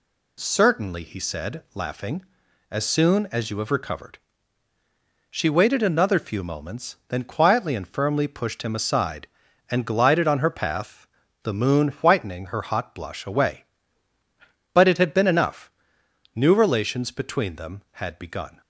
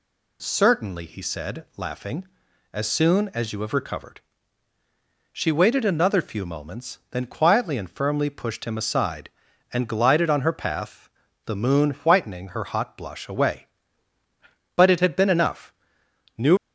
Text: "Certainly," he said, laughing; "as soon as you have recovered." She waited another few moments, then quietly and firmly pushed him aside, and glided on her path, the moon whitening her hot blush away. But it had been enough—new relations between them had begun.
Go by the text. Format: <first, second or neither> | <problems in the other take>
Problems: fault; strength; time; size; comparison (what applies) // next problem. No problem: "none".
first | stops before "relations between them had begun"; at 16.5 s